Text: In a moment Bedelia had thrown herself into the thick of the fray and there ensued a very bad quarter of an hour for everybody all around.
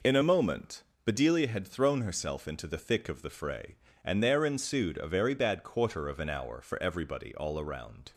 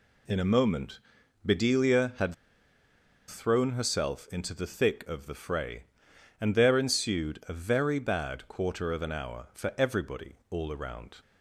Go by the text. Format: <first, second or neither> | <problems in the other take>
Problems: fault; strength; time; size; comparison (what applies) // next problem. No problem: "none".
first | pauses between "moment" and "Bedelia"; noticeable; at 0.9 s; 0.46 s long; slight in the first // pauses between "had" and "thrown"; noticeable; at 2.3 s; 0.93 s long